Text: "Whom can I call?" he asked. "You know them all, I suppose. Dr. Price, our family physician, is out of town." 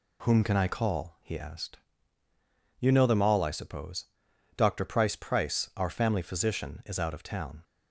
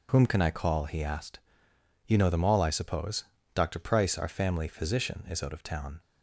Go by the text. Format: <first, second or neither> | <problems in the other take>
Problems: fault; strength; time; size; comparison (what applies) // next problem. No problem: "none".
second | says "Price" twice; at 5.1 s